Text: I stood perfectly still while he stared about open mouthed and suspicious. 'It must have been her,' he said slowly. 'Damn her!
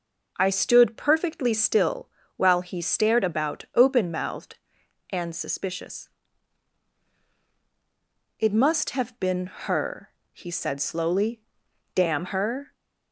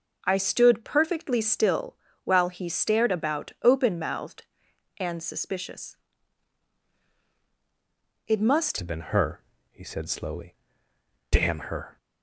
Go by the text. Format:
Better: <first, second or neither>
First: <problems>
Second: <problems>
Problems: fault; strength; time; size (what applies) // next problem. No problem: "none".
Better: first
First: pauses between "still" and "while"; slight; at 2.0 s; 0.28 s long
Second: pauses between "still" and "while"; slight; at 1.9 s; 0.28 s long // changes voice at "have"; from 8.7 s on; 3.2 s long